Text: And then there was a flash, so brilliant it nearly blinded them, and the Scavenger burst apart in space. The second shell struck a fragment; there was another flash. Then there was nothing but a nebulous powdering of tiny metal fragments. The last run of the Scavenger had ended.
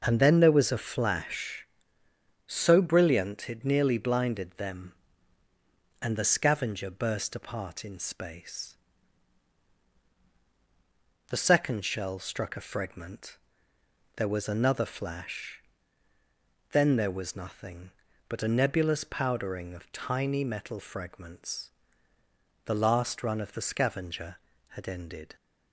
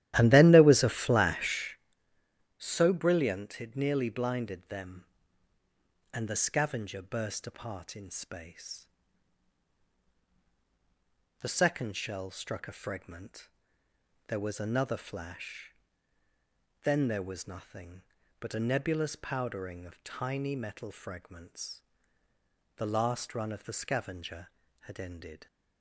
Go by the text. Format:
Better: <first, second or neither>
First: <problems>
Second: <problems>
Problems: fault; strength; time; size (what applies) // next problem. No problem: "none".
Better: first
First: none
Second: starts louder than the rest; strong; until 1.9 s; 13.5 dB